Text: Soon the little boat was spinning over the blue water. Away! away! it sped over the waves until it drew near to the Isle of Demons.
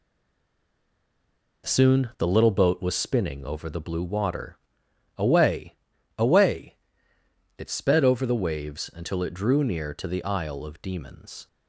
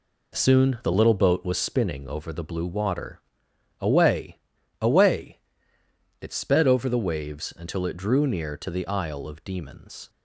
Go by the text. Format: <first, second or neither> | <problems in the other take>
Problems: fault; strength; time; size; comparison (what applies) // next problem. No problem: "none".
second | stays silent before the first word; noticeable; until 1.6 s; 1.6 s long